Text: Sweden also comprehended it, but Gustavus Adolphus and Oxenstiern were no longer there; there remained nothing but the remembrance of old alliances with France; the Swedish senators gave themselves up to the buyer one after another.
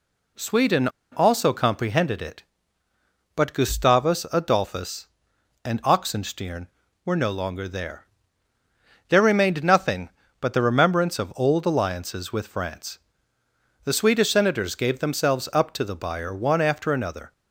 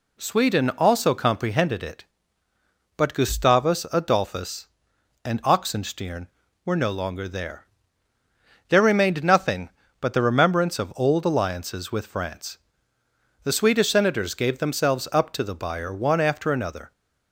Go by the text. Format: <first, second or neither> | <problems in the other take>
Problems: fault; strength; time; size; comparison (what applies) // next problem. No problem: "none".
second | pauses between "Sweden" and "also"; slight; at 0.8 s; 0.24 s long